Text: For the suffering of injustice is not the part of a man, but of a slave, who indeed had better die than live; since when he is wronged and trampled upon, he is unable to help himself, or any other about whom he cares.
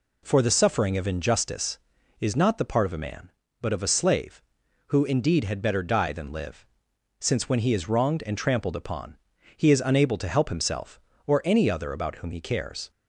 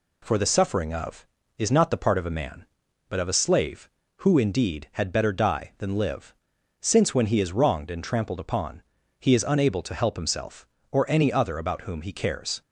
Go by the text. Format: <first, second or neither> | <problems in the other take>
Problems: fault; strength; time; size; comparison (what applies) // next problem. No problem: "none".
first | skips "injustice"; at 1.4 s